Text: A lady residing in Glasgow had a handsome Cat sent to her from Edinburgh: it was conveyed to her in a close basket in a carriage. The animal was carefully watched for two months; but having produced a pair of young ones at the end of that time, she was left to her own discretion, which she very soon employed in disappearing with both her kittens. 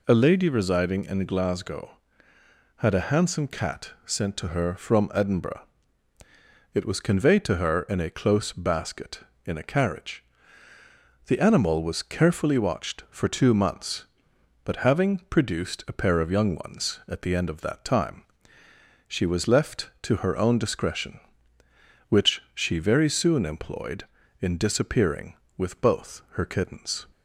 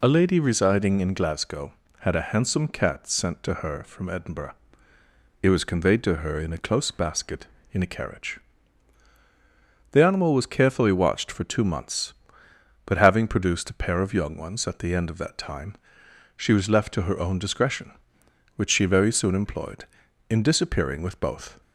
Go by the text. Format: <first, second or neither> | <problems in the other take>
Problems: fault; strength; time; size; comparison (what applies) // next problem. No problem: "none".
first | stops before "her kittens"; at 21.6 s